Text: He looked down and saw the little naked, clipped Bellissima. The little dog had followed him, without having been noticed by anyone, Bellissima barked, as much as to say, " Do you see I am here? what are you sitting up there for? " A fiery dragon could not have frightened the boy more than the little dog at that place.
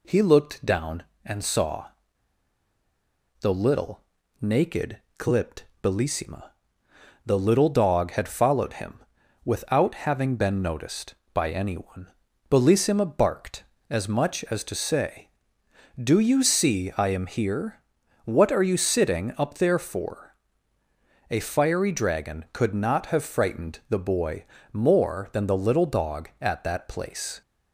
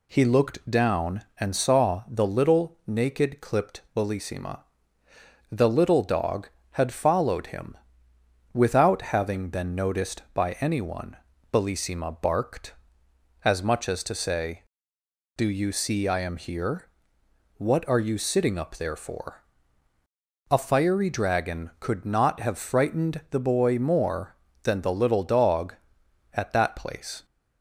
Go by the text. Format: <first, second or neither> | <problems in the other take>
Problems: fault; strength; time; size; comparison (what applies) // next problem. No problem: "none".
second | pauses between "saw" and "the"; strong; at 1.8 s; 1.5 s long // pauses between "little" and "naked"; at 4.0 s; 0.38 s long // pauses between "clipped" and "Bellissima"; slight; at 5.6 s; 0.18 s long // pauses between "boy" and "more"; slight; at 24.4 s; 0.26 s long